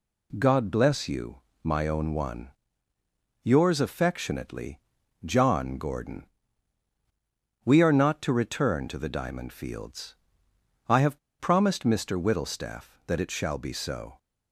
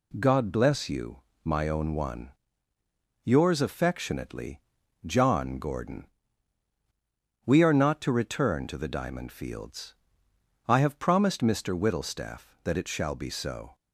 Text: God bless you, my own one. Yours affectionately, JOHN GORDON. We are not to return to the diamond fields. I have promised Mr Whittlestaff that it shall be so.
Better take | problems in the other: second | pauses between "have" and "promised"; slight; at 11.1 s; 0.20 s long

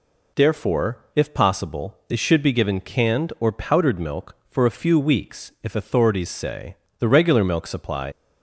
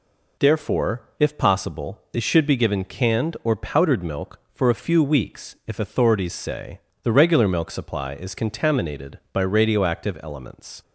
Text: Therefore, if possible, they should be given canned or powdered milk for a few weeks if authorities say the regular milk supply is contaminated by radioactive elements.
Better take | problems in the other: second | pauses between "say" and "the"; slight; at 6.7 s; 0.24 s long; slight in the second // stops before "is contaminated by radioactive elements"; at 8.1 s

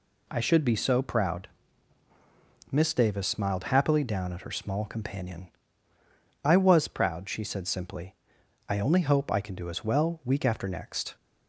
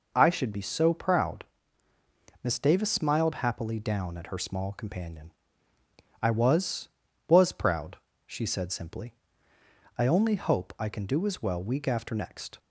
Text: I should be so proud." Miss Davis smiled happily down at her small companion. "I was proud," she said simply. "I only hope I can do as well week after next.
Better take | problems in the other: first | says "was" twice; at 7.3 s

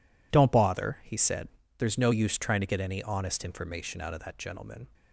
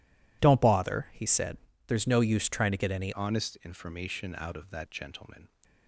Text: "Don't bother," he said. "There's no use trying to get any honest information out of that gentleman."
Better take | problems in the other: first | changes voice at "honest"; from 3.1 s on; 2.3 s long

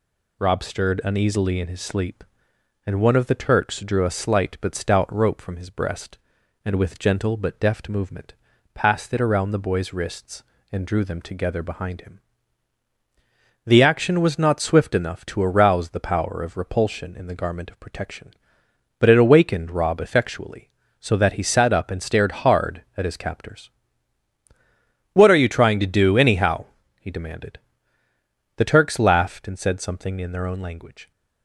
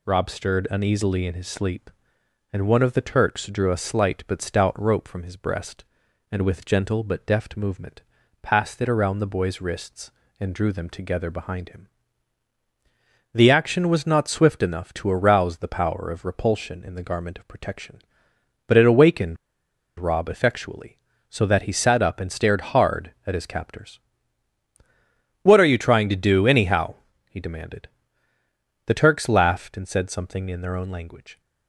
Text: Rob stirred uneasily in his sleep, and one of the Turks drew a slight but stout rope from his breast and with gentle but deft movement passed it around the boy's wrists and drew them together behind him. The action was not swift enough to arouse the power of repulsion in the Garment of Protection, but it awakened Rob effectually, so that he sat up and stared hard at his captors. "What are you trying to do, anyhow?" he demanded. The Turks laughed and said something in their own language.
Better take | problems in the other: first | pauses between "movement" and "passed"; at 8.0 s; 0.40 s long; also in the first // pauses between "awakened" and "Rob"; noticeable; at 19.3 s; 0.63 s long

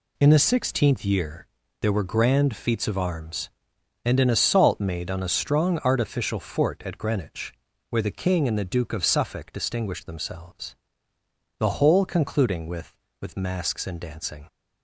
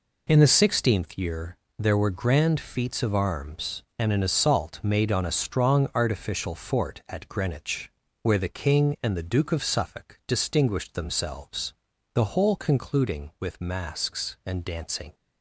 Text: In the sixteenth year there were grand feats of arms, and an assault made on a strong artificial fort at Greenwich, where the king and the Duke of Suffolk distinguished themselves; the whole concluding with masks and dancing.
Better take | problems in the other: second | pauses between "year" and "there"; slight; at 1.4 s; 0.36 s long; slight in the second // says "with" twice; at 13.1 s

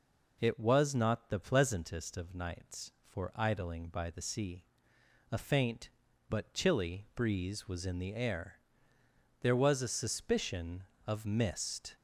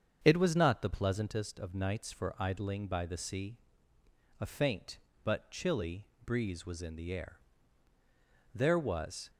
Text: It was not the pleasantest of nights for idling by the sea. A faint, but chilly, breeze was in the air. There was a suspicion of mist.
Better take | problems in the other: first | starts louder than the rest; strong; until 1.2 s; 7 dB // stops before "a suspicion of mist"; at 9.2 s

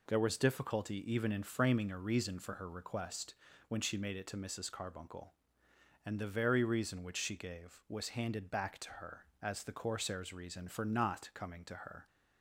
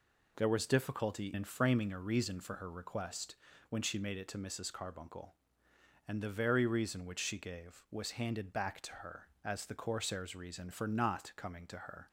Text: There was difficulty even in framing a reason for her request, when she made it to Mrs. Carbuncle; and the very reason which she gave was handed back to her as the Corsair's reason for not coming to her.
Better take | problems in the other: first | skips "even"; at 1.3 s

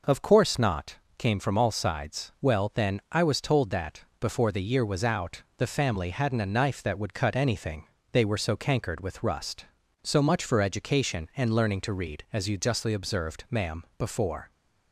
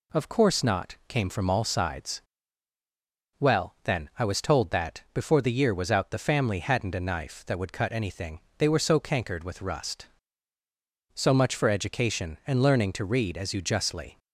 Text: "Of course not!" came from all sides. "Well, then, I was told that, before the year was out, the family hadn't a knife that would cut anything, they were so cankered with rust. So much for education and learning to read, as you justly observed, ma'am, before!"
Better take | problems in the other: first | stops before "observed ma'am before"; at 14.1 s

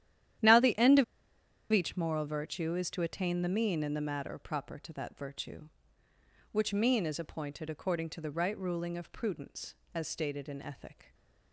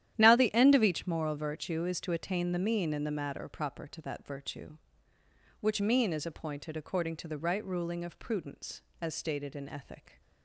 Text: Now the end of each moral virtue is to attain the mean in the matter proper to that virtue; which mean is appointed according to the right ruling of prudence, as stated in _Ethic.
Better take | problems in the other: second | starts louder than the rest; strong; until 2.0 s; 11.5 dB; strong in the second // pauses between "of" and "each"; noticeable; at 1.0 s; 0.67 s long

